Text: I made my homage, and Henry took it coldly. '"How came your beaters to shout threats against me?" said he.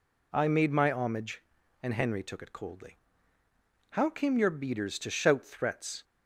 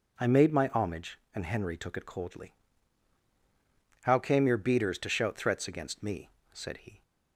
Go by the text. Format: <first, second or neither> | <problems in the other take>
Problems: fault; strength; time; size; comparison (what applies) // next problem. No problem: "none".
second | stops before "against me said he"; at 6.0 s